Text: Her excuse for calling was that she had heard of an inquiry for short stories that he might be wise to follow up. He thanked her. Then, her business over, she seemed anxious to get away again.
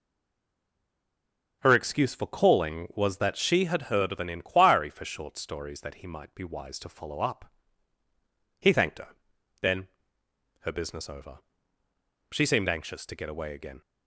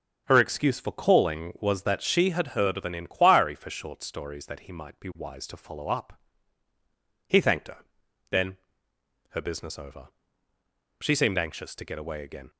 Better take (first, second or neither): second